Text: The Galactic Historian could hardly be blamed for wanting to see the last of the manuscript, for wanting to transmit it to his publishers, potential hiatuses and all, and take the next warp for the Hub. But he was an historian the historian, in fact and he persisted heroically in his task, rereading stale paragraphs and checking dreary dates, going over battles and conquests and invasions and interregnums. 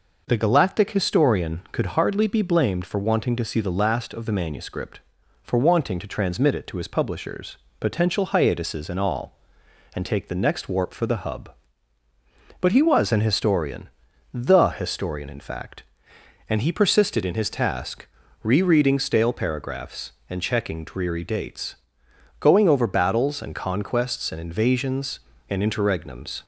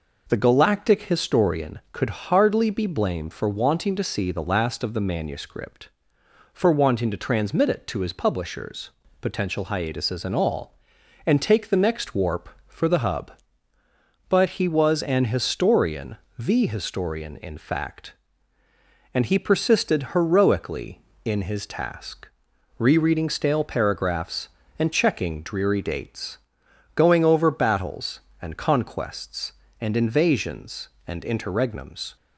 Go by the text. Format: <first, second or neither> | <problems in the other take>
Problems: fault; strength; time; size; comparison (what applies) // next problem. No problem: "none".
second | pauses between "historian" and "the"; at 13.8 s; 0.44 s long; slight in the second // skips "heroically"; at 17.2 s